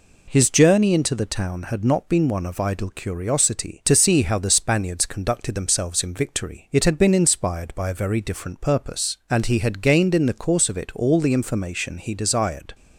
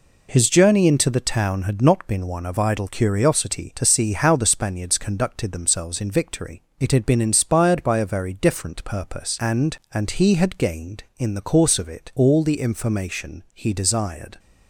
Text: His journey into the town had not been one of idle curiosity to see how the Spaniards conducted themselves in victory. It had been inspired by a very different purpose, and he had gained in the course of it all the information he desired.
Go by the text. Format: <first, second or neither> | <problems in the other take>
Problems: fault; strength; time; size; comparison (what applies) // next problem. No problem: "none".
first | says "and" twice; at 9.9 s